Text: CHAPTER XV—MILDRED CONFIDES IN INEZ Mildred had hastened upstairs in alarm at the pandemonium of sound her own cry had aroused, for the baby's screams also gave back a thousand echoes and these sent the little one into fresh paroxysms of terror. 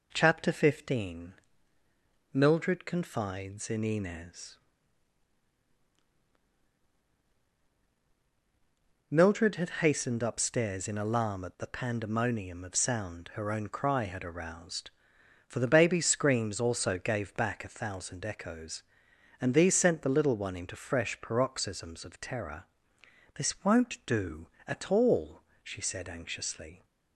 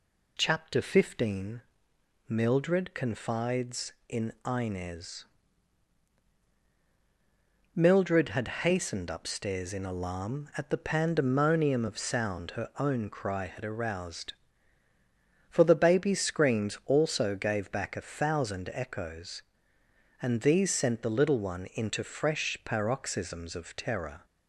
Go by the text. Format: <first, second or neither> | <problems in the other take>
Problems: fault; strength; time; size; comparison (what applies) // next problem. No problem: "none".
second | pauses between "INEZ" and "Mildred"; strong; at 4.5 s; 4.5 s long; strong in the second // goes on to say "This won't do at all she said anxiously"; strong; from 23.3 s on; 3.5 s long